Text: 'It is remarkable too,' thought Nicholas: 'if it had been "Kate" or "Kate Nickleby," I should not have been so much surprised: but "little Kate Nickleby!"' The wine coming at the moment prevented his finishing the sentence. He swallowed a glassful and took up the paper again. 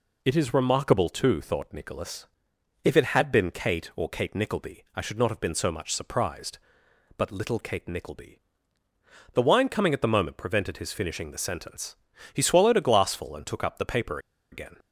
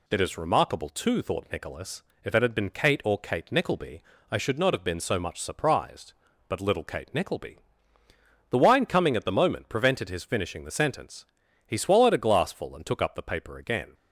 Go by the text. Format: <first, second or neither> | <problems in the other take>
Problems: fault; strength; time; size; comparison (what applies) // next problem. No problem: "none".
second | pauses between "paper" and "again"; slight; at 14.1 s; 0.33 s long